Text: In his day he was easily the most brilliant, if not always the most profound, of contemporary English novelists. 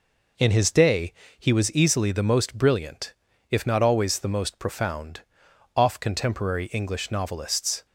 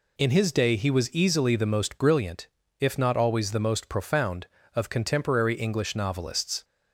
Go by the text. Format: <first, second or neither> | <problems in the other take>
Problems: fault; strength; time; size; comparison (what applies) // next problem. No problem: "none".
second | pauses between "day" and "he"; slight; at 1.1 s; 0.26 s long // says "off" for "of"; at 5.7 s